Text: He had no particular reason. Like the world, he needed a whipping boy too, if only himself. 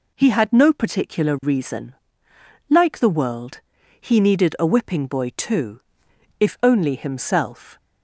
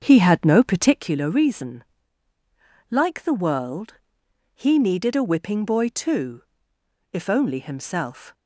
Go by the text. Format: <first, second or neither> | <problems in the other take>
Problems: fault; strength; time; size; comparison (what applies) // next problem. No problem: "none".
first | starts louder than the rest; until 1.2 s; 7 dB